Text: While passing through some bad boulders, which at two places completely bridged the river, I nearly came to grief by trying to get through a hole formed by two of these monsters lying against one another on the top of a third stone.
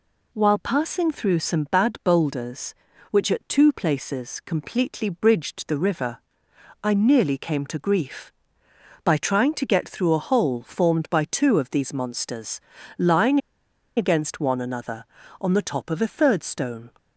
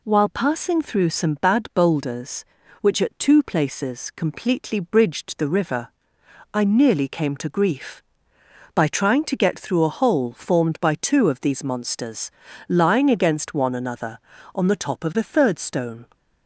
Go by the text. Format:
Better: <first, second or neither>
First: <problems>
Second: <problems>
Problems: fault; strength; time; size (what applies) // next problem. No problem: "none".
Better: second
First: pauses between "monsters" and "lying"; slight; at 12.6 s; 0.36 s long // pauses between "lying" and "against"; noticeable; at 13.3 s; 0.57 s long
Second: pauses between "monsters" and "lying"; slight; at 12.3 s; 0.36 s long